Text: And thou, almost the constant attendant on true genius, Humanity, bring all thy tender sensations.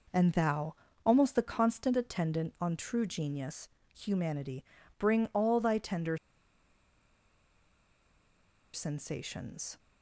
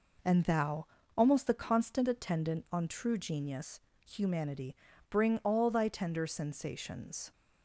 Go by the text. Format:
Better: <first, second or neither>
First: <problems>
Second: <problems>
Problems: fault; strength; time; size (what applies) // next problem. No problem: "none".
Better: second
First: pauses between "tender" and "sensations"; strong; at 6.1 s; 2.5 s long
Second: none